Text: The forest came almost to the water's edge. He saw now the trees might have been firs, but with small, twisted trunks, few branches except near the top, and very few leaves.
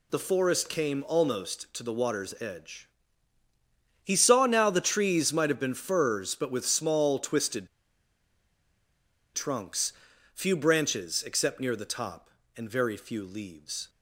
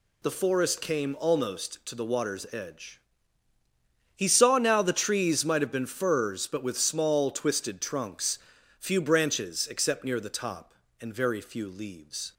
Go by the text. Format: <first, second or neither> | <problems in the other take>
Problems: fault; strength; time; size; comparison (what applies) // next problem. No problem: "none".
second | pauses between "twisted" and "trunks"; strong; at 7.6 s; 1.6 s long